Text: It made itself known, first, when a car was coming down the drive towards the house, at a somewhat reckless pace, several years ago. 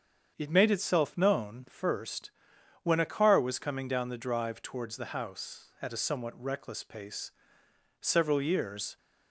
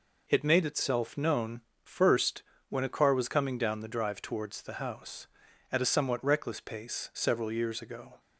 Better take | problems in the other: second | starts louder than the rest; strong; until 1.3 s; 7.5 dB // stops before "ago"; at 8.9 s

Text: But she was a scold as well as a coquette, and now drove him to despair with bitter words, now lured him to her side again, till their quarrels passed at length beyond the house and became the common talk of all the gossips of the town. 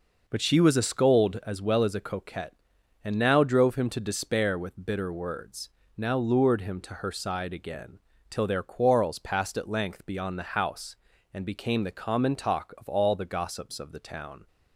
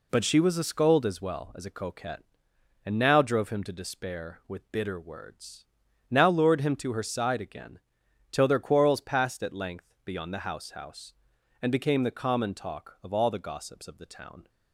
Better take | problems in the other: first | says "house" twice; at 10.7 s

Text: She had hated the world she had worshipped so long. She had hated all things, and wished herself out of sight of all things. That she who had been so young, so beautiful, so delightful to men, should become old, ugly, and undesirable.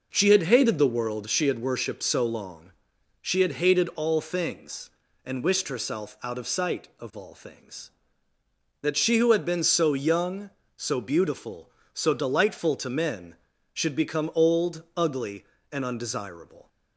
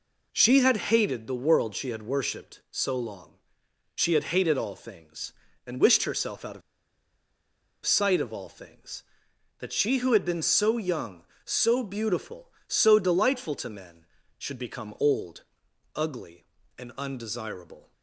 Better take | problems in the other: first | pauses between "of" and "sight"; strong; at 6.6 s; 1.2 s long

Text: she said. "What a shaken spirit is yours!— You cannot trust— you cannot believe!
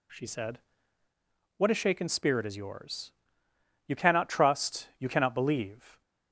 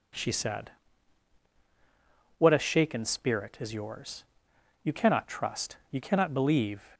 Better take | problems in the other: neither | none

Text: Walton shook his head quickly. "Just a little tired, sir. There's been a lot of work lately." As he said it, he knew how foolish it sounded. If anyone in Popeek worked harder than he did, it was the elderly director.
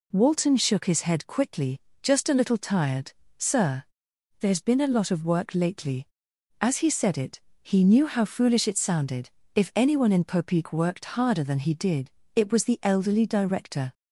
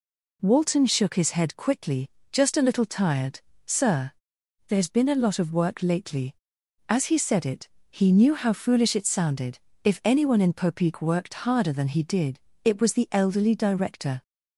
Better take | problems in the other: neither | none

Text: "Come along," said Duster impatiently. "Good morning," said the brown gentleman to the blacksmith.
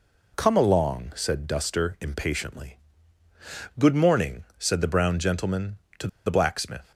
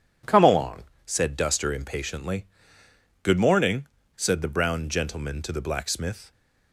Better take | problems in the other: second | pauses between "to" and "the"; slight; at 6.0 s; 0.17 s long

